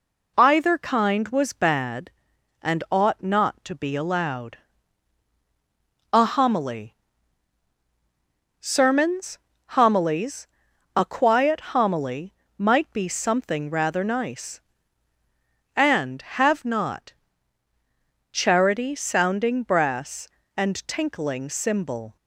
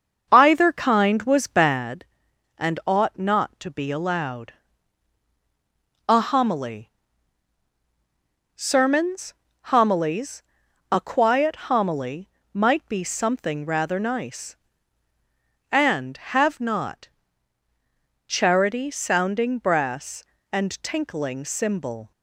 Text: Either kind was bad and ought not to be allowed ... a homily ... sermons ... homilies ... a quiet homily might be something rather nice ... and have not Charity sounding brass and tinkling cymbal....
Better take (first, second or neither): first